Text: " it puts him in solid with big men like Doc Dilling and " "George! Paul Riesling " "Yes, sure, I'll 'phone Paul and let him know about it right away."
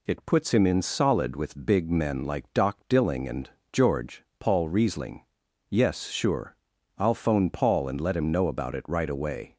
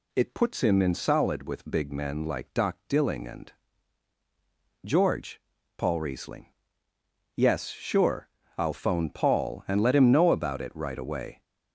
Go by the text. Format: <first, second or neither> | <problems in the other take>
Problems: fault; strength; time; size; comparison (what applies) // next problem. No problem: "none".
neither | none